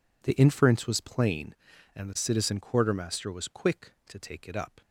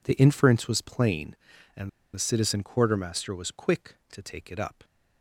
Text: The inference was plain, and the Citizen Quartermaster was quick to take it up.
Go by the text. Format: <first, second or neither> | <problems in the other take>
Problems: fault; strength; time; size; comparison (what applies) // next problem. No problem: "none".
first | pauses between "and" and "the"; slight; at 1.8 s; 0.25 s long